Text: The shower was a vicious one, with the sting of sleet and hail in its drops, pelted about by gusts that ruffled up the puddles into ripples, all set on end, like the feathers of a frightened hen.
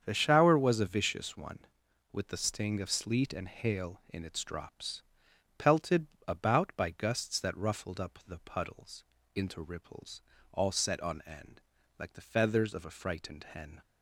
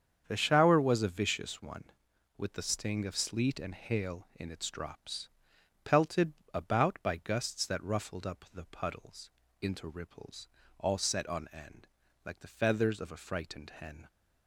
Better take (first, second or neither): neither